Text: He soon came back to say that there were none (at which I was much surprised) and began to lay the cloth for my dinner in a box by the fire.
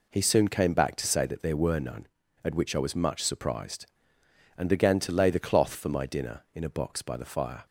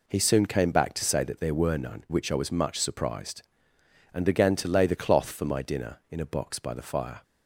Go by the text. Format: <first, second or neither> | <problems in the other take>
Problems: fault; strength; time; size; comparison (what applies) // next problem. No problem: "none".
first | skips "at"; at 2.0 s